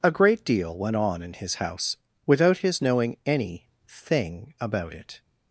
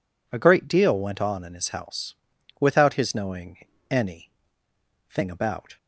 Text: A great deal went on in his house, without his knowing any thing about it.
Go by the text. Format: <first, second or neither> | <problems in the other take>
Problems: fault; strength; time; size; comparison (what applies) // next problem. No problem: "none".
first | pauses between "knowing" and "any"; slight; at 3.5 s; 0.30 s long // pauses between "any" and "thing"; noticeable; at 4.2 s; 0.80 s long; slight in the first // stops before "it"; at 5.7 s